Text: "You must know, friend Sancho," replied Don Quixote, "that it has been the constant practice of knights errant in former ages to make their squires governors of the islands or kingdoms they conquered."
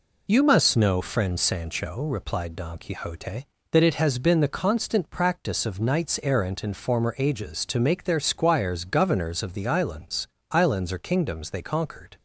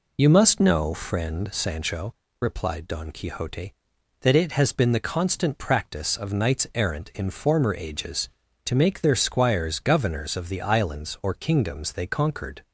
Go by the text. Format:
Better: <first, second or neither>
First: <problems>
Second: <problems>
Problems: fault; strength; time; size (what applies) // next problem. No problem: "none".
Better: second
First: says "islands" twice; at 10.5 s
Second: none